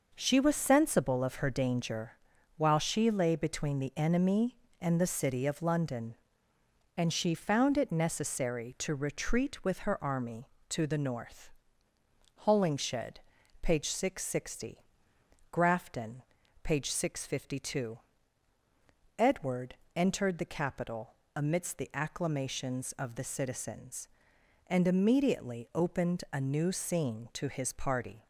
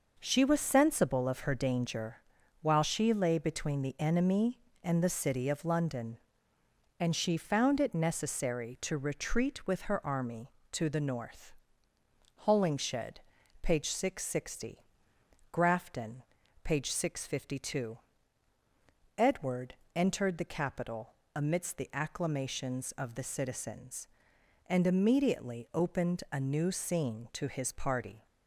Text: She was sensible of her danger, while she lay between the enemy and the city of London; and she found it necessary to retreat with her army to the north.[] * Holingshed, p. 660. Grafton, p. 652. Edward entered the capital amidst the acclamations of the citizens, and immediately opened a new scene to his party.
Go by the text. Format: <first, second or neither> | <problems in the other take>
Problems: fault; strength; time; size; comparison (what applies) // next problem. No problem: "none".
neither | pauses between "Edward" and "entered"; slight; the same in both // pauses between "capital" and "amidst"; slight; the same in both